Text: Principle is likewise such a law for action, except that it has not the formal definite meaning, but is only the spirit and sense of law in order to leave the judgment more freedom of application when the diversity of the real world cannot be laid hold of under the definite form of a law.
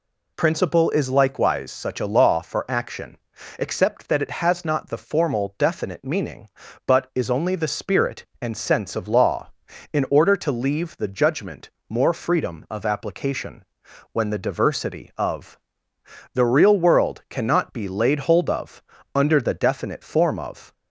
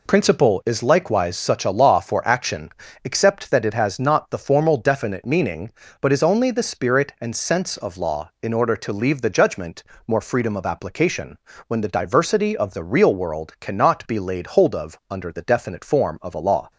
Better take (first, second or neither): second